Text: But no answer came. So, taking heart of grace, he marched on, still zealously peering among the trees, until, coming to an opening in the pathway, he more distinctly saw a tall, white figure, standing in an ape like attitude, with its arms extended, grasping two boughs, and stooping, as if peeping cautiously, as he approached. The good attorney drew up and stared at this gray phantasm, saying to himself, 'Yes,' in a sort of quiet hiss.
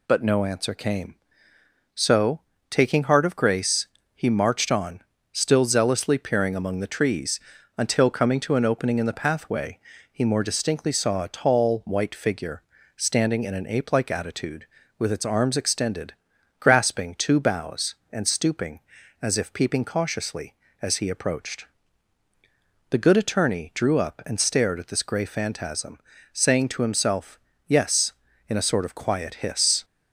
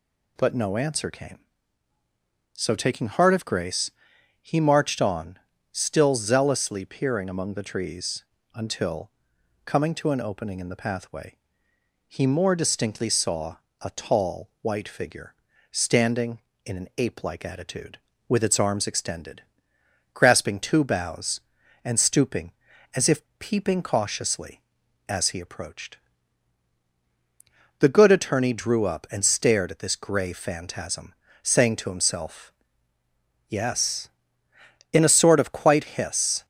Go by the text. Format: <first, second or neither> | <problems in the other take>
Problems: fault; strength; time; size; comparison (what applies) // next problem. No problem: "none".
first | pauses between "saw" and "a"; slight; at 13.5 s; 0.24 s long // pauses between "if" and "peeping"; slight; at 23.2 s; 0.18 s long // says "quite" for "quiet"; at 35.5 s